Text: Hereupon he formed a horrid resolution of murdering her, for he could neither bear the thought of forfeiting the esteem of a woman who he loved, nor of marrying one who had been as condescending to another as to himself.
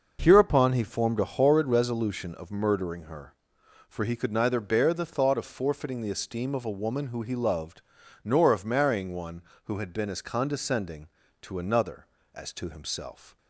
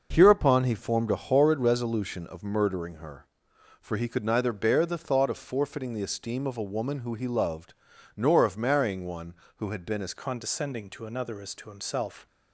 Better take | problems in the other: first | changes voice at "condescending"; from 10.1 s on; 2.1 s long

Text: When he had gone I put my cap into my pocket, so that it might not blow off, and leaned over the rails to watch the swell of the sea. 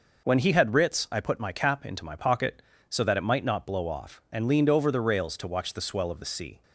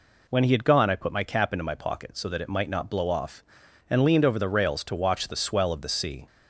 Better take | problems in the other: second | says "writs" for "gone"; at 0.7 s

